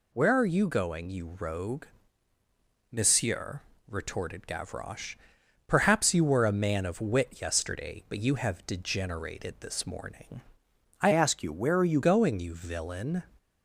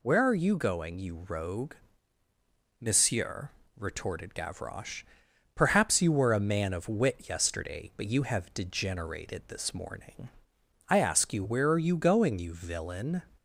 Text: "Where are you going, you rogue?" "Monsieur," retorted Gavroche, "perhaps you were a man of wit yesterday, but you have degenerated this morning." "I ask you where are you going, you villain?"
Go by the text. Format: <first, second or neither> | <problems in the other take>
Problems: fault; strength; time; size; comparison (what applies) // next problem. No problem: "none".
second | changes voice from "ask" to "you"; from 11.1 to 11.9 s; 0.8 s long